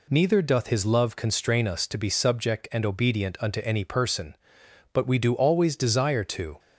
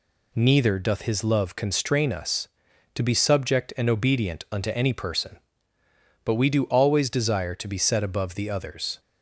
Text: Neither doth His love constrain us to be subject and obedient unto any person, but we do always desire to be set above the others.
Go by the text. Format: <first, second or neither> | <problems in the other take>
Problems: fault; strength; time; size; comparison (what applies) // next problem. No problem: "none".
second | stops before "be set above the others"; at 6.5 s